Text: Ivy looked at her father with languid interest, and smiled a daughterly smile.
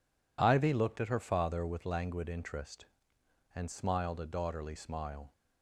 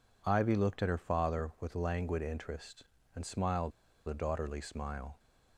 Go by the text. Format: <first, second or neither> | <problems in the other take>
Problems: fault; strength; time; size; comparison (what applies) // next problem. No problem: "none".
first | pauses between "smiled" and "a"; at 3.7 s; 0.37 s long